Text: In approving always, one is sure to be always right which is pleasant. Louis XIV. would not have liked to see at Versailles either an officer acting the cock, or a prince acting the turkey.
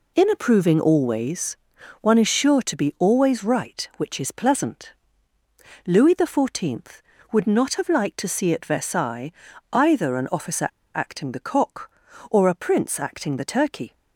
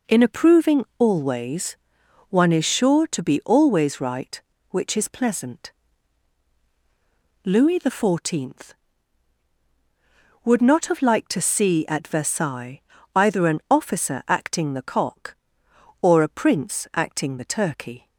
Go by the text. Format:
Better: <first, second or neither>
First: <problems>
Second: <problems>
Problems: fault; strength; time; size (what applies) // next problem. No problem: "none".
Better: second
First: pauses between "Versailles" and "either"; at 9.3 s; 0.40 s long // pauses between "officer" and "acting"; slight; at 10.6 s; 0.26 s long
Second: pauses between "Versailles" and "either"; slight; at 12.8 s; 0.34 s long